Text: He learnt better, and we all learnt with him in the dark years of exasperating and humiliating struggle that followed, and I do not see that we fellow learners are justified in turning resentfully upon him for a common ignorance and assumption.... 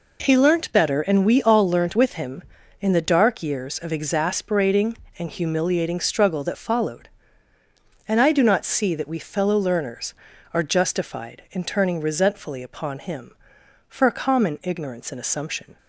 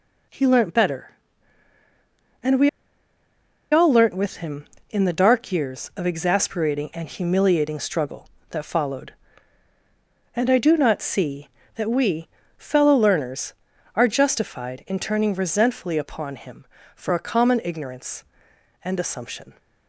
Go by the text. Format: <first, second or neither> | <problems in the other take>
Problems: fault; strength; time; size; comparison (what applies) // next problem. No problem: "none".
first | pauses between "we" and "all"; at 2.6 s; 1.0 s long // pauses between "we" and "fellow"; slight; at 12.2 s; 0.30 s long